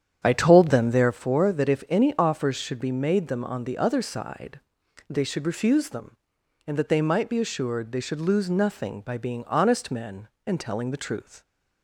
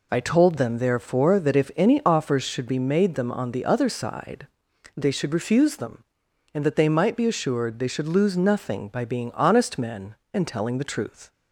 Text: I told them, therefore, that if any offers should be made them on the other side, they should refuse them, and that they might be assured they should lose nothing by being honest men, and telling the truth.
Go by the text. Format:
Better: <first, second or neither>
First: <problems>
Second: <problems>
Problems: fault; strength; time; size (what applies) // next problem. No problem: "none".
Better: second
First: starts louder than the rest; strong; until 1.2 s; 9 dB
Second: none